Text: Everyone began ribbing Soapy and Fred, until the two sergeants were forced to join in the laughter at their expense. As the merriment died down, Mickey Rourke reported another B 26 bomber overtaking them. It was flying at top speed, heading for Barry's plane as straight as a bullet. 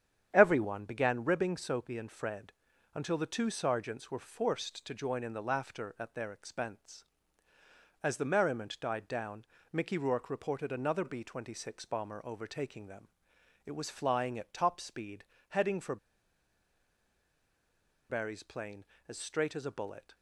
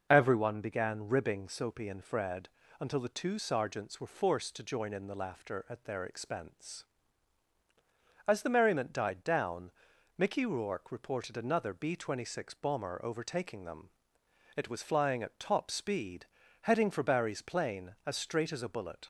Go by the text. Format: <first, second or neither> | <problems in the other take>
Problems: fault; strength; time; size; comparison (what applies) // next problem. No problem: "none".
second | starts louder than the rest; strong; until 1.3 s; 9 dB // pauses between "for" and "Barry's"; strong; at 15.9 s; 2.1 s long